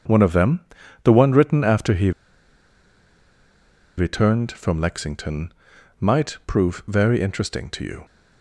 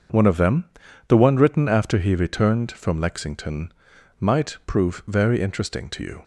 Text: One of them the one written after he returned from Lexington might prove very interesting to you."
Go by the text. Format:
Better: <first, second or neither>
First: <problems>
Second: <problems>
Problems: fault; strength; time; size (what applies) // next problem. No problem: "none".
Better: second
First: starts louder than the rest; until 1.4 s; 6.5 dB // pauses between "them" and "the"; at 0.6 s; 0.42 s long // pauses between "he" and "returned"; strong; at 2.1 s; 1.8 s long // pauses between "Lexington" and "might"; noticeable; at 5.5 s; 0.46 s long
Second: starts louder than the rest; until 1.5 s; 6.5 dB // pauses between "them" and "the"; at 0.6 s; 0.42 s long // pauses between "Lexington" and "might"; noticeable; at 3.7 s; 0.46 s long